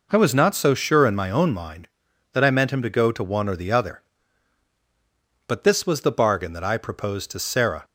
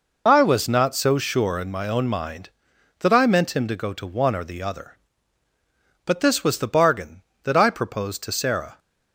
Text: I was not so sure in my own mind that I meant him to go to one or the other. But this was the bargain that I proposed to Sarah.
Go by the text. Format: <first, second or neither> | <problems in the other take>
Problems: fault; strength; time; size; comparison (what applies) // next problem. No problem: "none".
first | loses the start of "I"; at 0.2 s; 35 ms